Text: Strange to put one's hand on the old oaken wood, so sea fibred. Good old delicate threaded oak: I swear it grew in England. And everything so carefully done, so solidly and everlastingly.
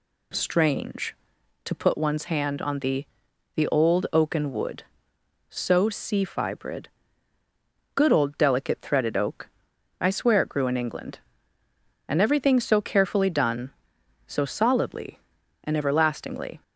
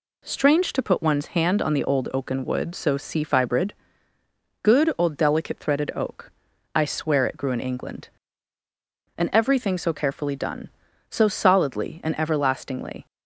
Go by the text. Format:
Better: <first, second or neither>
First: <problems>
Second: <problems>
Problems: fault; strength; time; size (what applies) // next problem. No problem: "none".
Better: second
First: says "the" twice; at 3.5 s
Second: none